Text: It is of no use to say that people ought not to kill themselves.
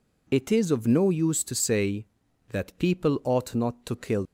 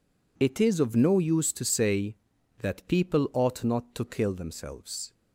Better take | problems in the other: second | stops before "themselves"; at 4.2 s

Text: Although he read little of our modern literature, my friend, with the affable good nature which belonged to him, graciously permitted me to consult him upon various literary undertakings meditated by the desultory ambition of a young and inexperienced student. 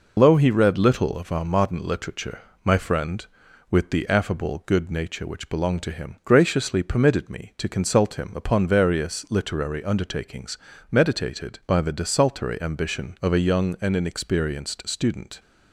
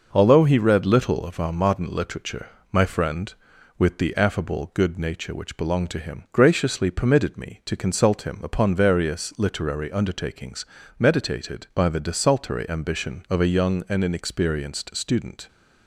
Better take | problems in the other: second | loses the start of "Although"; at 0.1 s; 145 ms // pauses between "undertakings" and "meditated"; slight; at 10.5 s; 0.34 s long; slight in the second

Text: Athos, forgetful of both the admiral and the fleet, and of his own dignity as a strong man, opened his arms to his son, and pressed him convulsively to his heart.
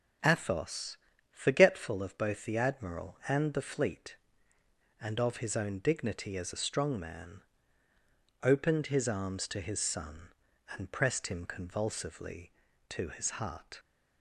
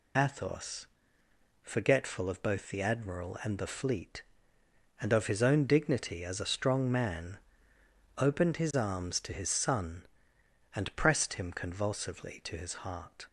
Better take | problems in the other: first | loses the start of "Athos"; at 0.1 s; 35 ms

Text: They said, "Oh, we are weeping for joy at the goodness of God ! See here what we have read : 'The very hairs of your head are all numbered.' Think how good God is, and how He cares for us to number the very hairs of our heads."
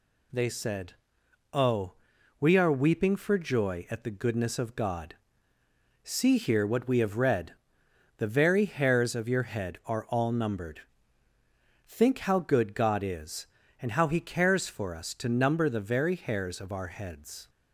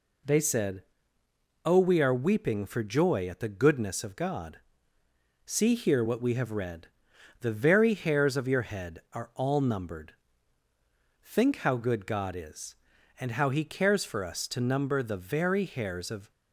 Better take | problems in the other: first | stops before "our heads"; at 16.3 s

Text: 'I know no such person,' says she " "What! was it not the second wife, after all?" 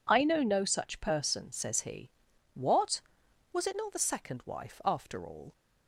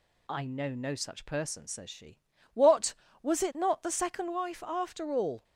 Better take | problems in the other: second | says "he" for "she"; at 1.8 s

